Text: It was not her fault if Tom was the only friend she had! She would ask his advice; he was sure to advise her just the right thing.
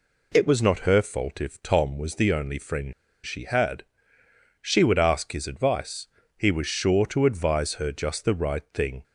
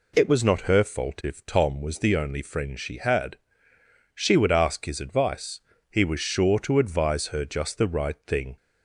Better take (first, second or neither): second